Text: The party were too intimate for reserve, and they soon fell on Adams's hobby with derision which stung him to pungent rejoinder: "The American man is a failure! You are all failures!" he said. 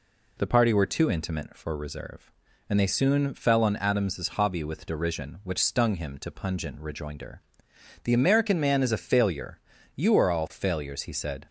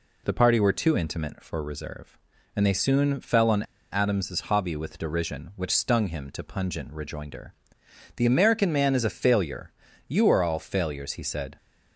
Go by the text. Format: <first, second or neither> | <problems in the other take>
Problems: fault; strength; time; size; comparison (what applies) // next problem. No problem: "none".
first | pauses between "on" and "Adams's"; slight; at 3.6 s; 0.28 s long